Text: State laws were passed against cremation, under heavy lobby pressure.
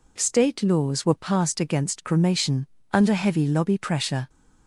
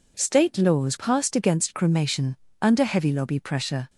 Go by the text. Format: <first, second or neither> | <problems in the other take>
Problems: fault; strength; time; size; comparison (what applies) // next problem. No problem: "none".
first | skips "were"; at 0.9 s